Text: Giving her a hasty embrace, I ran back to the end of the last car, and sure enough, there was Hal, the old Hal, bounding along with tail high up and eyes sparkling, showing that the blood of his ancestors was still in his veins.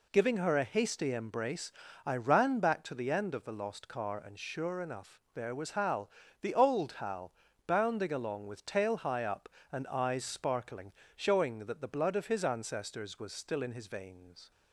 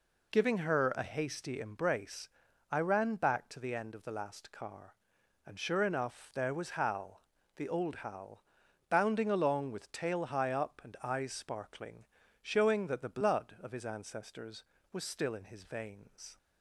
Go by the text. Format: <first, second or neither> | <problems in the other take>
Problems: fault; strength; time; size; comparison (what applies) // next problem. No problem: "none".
second | says "lost" for "last"; at 3.5 s